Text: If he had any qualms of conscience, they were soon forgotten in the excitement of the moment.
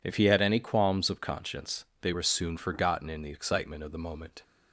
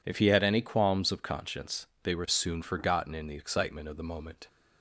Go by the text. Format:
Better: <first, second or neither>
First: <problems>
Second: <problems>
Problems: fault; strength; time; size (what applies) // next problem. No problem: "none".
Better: neither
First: none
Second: none